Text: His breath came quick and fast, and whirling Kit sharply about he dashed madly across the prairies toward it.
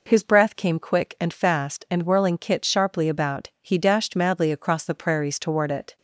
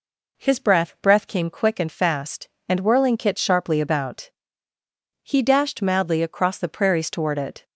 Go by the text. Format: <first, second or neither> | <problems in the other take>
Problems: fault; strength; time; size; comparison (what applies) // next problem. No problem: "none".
first | says "breath" twice; at 1.0 s // pauses between "about" and "he"; noticeable; at 4.3 s; 0.96 s long